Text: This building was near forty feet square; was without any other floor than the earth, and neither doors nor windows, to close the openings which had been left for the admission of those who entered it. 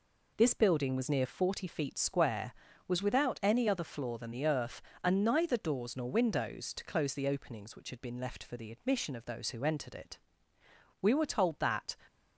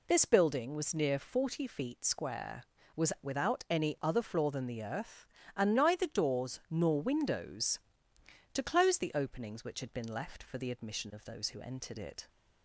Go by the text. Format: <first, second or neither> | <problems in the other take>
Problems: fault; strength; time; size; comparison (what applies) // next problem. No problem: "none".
second | goes on to say "We were told that"; noticeable; from 11.0 s on; 0.96 s long